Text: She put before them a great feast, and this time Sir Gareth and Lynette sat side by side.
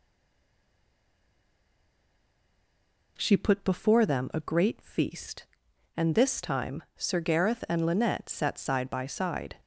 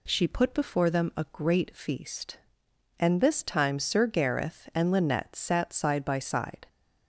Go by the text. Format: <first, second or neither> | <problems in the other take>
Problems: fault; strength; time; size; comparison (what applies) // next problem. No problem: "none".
second | stays silent before the first word; strong; until 3.1 s; 3.1 s long